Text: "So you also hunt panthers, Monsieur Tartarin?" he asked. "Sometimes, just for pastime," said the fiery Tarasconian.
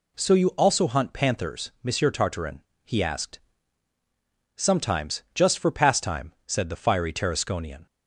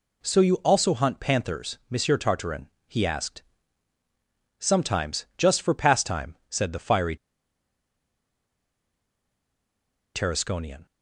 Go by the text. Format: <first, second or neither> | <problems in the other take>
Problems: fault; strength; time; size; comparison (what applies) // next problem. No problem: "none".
first | pauses between "fiery" and "Tarasconian"; strong; at 7.1 s; 2.9 s long